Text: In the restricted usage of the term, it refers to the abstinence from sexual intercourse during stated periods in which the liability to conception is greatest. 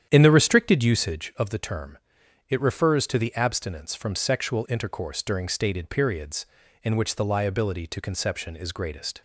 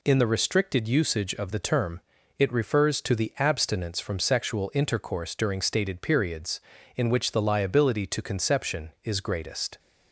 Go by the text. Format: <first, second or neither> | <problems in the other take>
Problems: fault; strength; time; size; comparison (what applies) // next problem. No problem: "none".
second | starts louder than the rest; strong; until 1.3 s; 9.5 dB